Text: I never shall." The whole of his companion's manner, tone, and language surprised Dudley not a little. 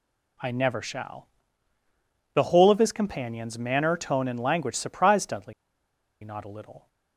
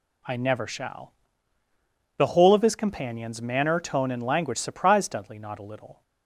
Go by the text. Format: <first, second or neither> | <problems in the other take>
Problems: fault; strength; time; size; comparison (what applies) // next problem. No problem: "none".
second | pauses between "Dudley" and "not"; noticeable; at 5.5 s; 0.70 s long